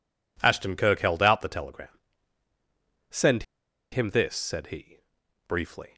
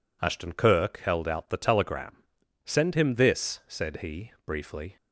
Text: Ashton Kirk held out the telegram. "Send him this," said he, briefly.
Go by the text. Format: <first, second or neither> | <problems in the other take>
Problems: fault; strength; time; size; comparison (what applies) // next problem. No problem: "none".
second | pauses between "Send" and "him"; noticeable; at 3.4 s; 0.48 s long